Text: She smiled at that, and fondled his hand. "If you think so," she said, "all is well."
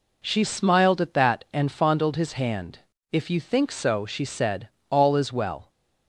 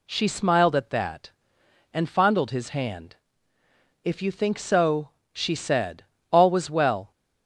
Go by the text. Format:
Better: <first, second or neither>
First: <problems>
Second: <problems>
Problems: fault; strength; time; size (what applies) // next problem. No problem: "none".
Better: first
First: none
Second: says "was" for "is"; at 6.4 s